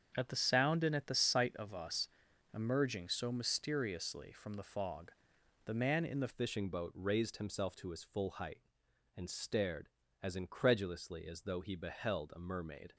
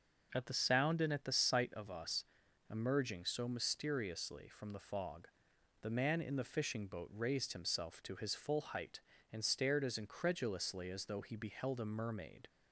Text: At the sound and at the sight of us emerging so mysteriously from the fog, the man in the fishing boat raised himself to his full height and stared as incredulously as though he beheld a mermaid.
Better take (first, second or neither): second